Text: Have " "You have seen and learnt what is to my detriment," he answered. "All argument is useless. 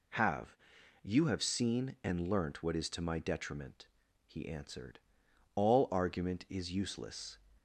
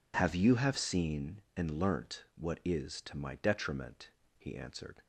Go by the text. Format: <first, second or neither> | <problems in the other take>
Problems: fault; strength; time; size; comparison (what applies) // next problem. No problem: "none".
first | stops before "All argument is useless"; at 5.0 s